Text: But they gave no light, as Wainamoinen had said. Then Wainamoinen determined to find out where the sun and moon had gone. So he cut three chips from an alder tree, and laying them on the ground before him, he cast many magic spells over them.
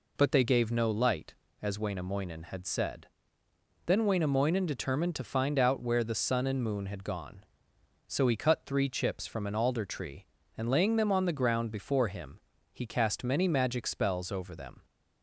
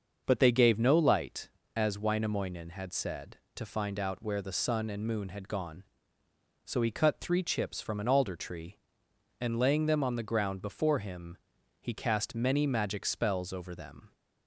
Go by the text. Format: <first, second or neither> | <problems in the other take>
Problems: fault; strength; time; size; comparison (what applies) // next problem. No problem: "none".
first | starts louder than the rest; until 1.2 s; 6.5 dB // skips "Then Wainamoinen determined"; at 3.4 s